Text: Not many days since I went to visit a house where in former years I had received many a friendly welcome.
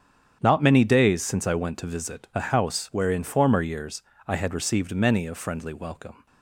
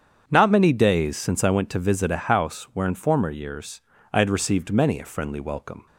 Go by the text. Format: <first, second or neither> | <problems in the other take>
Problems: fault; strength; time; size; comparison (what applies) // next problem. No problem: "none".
neither | starts louder than the rest; strong; the same in both // pauses between "years" and "I"; slight; the same in both